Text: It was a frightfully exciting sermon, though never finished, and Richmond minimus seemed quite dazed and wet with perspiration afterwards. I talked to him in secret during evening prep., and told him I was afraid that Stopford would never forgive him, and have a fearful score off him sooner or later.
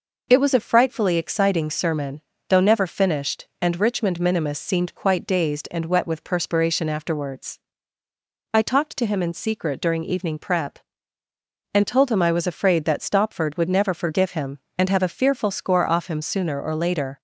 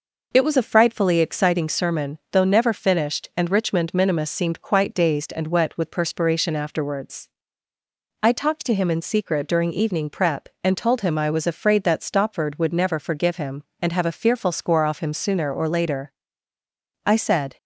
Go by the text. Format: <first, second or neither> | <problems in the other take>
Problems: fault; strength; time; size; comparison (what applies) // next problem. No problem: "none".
first | goes on to say "I said"; from 17.0 s on; 0.52 s long